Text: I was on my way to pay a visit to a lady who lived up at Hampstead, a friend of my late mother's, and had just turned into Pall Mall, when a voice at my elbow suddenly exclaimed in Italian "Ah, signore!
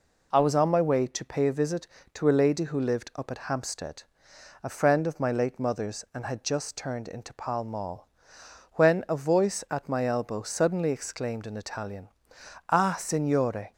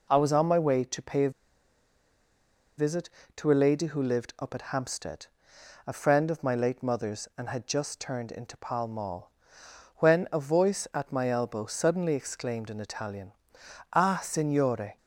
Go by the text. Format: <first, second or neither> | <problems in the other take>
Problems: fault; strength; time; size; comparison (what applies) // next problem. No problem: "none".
first | pauses between "a" and "visit"; strong; at 1.2 s; 1.4 s long // pauses between "Italian" and "Ah"; noticeable; at 13.3 s; 0.60 s long; noticeable in the first